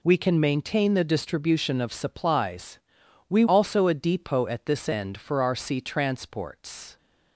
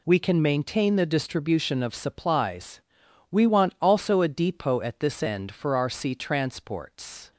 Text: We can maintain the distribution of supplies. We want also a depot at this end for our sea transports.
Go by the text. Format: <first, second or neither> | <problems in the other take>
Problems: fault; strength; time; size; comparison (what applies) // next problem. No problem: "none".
second | skips "want"; at 3.4 s